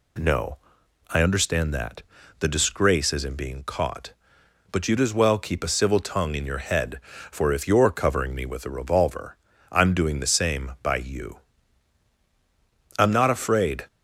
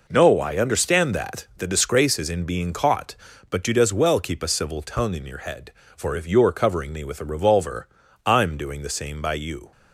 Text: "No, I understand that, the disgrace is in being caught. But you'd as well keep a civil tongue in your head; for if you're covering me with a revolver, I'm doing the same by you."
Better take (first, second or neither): second